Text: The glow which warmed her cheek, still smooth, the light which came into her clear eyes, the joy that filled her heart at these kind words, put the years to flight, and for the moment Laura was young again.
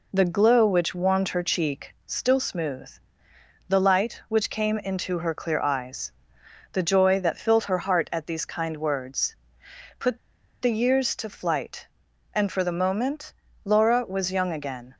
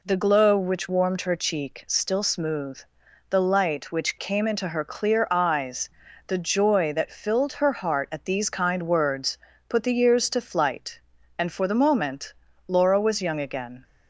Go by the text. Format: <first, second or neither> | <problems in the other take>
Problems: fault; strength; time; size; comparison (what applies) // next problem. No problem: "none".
second | pauses between "put" and "the"; at 10.1 s; 0.44 s long // pauses between "moment" and "Laura"; slight; at 13.3 s; 0.32 s long; slight in the second